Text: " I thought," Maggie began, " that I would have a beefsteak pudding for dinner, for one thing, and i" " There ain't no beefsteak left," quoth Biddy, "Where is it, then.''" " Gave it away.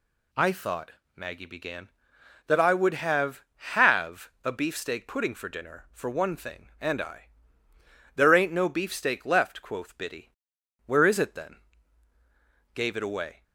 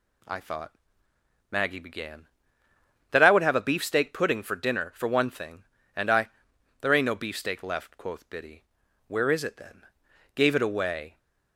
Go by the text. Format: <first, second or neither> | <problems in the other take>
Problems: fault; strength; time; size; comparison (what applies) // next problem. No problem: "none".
second | says "have" twice; at 3.7 s